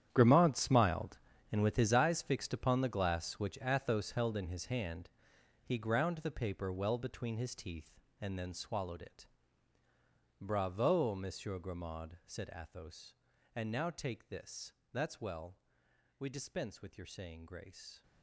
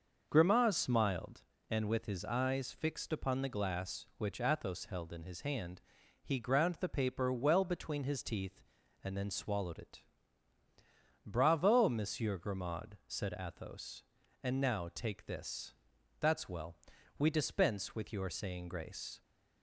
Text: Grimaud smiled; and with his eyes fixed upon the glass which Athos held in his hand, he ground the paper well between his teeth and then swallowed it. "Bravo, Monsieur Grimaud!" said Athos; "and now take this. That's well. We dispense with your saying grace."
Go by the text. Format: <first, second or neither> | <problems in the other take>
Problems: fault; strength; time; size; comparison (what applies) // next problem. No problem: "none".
second | gets quieter; strong; throughout; 14.5 dB // starts louder than the rest; strong; until 1.1 s; 10 dB; noticeable in the second